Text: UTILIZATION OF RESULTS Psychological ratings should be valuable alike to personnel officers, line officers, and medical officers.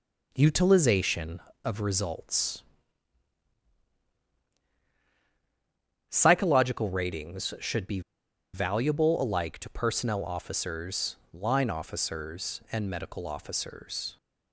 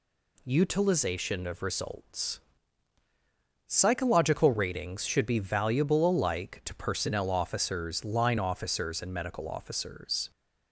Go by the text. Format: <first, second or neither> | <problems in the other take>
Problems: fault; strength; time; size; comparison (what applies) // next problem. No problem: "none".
second | pauses between "RESULTS" and "Psychological"; strong; at 2.6 s; 3.4 s long; strong in the second // pauses between "be" and "valuable"; noticeable; at 7.9 s; 0.53 s long